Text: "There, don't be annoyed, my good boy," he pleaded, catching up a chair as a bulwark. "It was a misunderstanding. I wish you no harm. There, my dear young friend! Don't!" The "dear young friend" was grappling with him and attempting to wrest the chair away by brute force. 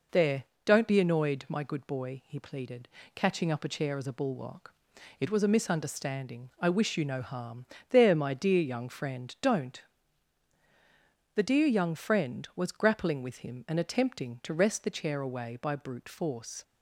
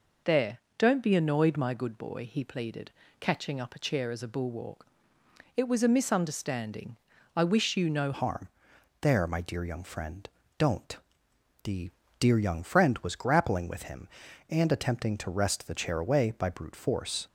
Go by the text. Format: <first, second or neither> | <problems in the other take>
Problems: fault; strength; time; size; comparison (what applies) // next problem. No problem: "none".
first | changes voice at "harm"; from 8.1 s on; 9.1 s long // pauses between "The" and "dear"; slight; at 11.9 s; 0.30 s long